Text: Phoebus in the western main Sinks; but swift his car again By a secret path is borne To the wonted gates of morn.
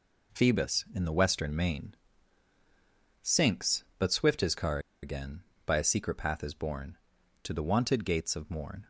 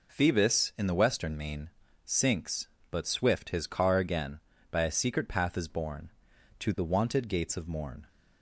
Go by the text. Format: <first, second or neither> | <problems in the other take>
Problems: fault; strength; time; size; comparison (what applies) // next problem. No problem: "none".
second | pauses between "main" and "Sinks"; strong; at 1.9 s; 1.2 s long; slight in the second // pauses between "car" and "again"; slight; at 4.7 s; 0.23 s long